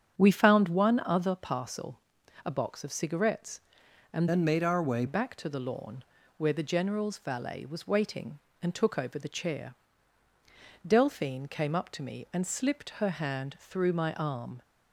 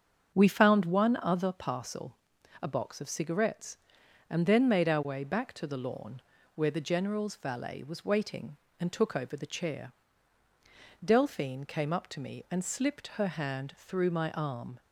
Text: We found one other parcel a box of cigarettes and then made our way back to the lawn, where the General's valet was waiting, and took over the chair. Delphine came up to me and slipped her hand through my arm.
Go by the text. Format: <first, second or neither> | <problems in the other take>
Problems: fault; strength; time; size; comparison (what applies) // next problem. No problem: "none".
second | starts louder than the rest; strong; until 1.2 s; 8 dB; also in the second // pauses between "parcel" and "a"; noticeable; at 1.9 s; 0.46 s long; noticeable in the second // changes voice from "then" to "way"; from 4.2 to 5.0 s; 0.8 s long